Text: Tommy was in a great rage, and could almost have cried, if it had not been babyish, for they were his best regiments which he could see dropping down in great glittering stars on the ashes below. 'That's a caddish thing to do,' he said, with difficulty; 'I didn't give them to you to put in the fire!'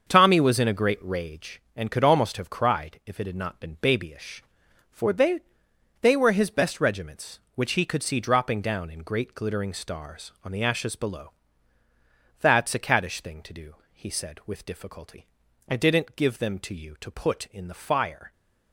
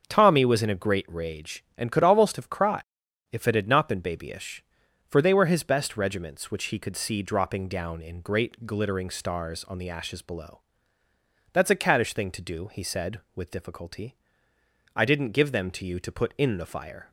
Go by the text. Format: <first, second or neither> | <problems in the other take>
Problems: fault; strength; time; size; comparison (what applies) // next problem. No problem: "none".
second | starts louder than the rest; until 1.1 s; 6.5 dB; also in the second // says "they" twice; at 5.9 s